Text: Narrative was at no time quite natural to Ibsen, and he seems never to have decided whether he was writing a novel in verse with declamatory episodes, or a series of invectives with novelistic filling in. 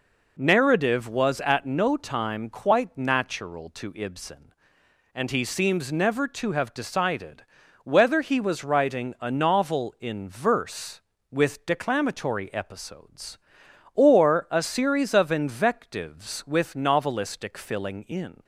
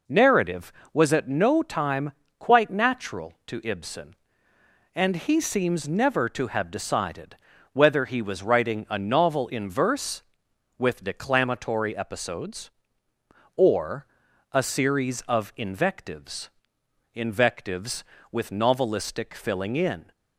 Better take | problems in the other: first | pauses between "time" and "quite"; slight; at 2.1 s; 0.26 s long // pauses between "decided" and "whether"; at 7.3 s; 0.38 s long; also in the first // pauses between "or" and "a"; noticeable; at 14.0 s; 0.46 s long // says "invectives" twice; at 17.1 s

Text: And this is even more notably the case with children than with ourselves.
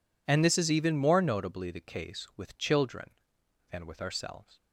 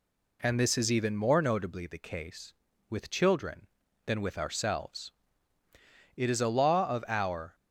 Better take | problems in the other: first | goes on to say "It is a law of our"; from 6.1 s on; 1.3 s long

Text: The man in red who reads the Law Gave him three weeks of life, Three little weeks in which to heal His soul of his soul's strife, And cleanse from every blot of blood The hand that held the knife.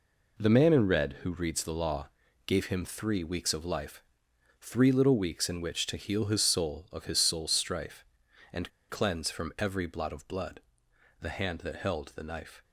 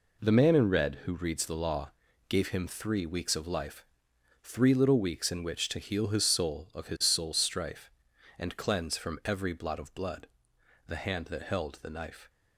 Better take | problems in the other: second | pauses between "Law" and "Gave"; at 2.0 s; 0.38 s long; also in the second // pauses between "And" and "cleanse"; slight; at 8.6 s; 0.20 s long // pauses between "blood" and "The"; noticeable; at 10.6 s; 0.60 s long; noticeable in the second

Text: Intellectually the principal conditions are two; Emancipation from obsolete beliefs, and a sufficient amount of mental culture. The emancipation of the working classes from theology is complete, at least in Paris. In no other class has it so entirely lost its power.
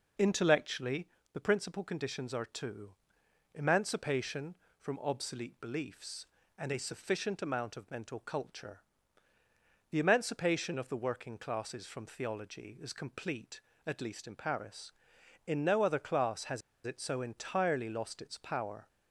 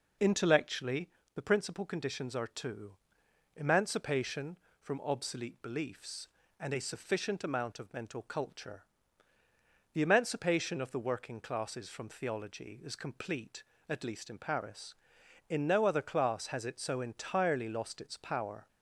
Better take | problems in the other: second | pauses between "Intellectually" and "the"; slight; at 1.0 s; 0.24 s long; slight in the second // pauses between "has" and "it"; slight; at 16.6 s; 0.25 s long

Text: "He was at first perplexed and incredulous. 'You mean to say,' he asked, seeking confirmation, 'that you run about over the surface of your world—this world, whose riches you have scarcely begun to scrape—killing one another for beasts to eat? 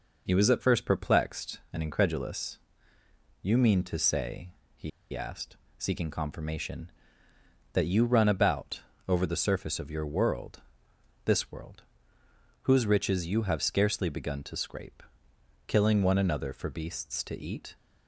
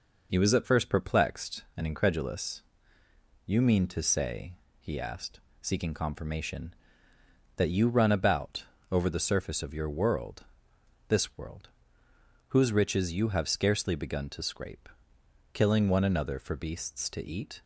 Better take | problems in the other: second | pauses between "he" and "asked"; slight; at 4.9 s; 0.23 s long // pauses between "about" and "over"; slight; at 8.7 s; 0.30 s long; slight in the second

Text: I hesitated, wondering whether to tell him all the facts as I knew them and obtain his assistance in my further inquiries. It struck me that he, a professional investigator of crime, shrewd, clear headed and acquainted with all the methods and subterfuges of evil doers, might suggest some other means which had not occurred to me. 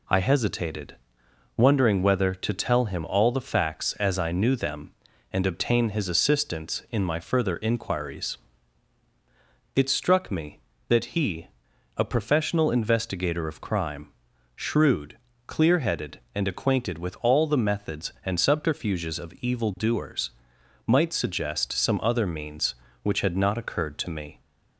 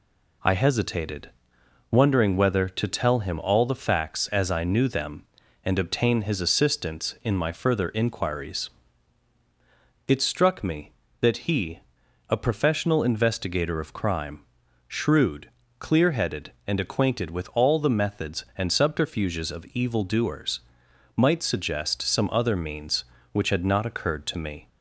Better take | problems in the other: neither | none

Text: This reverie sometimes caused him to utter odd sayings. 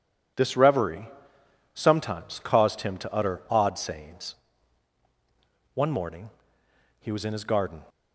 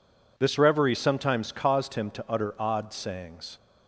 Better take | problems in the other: second | pauses between "reverie" and "sometimes"; noticeable; at 1.0 s; 0.64 s long // goes on to say "One morning he was in his garden"; strong; from 5.7 s on; 2.0 s long

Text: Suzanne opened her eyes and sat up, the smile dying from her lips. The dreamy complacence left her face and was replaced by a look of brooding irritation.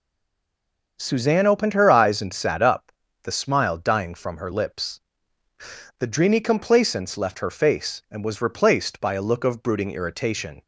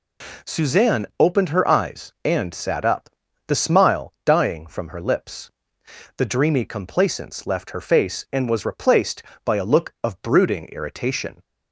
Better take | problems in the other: second | stays silent before the first word; until 0.9 s; 0.9 s long // starts louder than the rest; until 2.0 s; 6.5 dB

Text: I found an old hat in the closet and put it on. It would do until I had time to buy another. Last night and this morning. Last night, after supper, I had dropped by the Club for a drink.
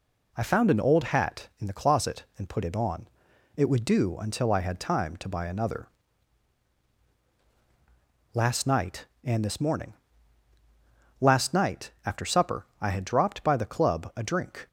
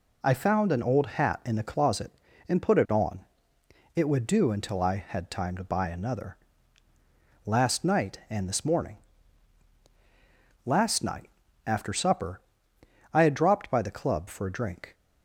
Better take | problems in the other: second | skips "for"; at 14.1 s

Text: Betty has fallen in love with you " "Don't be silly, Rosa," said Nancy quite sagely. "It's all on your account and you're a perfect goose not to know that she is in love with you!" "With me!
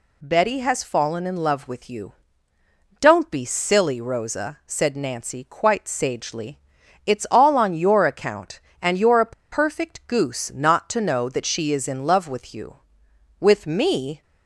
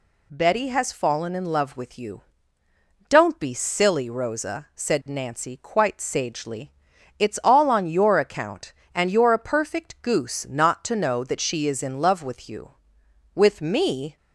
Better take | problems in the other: second | pauses between "a" and "perfect"; slight; at 9.3 s; 0.19 s long

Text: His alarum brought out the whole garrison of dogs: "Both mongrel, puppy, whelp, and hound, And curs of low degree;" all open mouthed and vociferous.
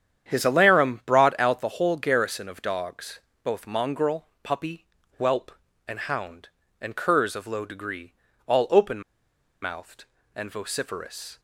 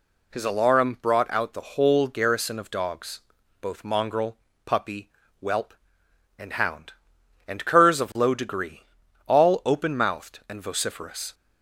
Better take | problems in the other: second | starts louder than the rest; strong; until 1.3 s; 9 dB // pauses between "open" and "mouthed"; noticeable; at 9.0 s; 0.61 s long

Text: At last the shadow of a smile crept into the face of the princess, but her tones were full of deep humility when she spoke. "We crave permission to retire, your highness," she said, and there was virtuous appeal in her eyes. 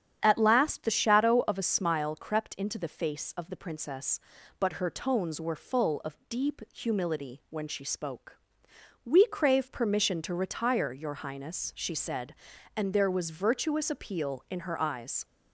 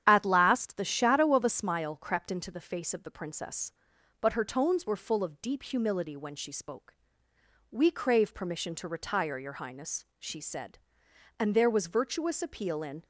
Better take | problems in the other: first | starts louder than the rest; strong; until 1.0 s; 9.5 dB; strong in the first // stops before "her eyes"; at 13.0 s

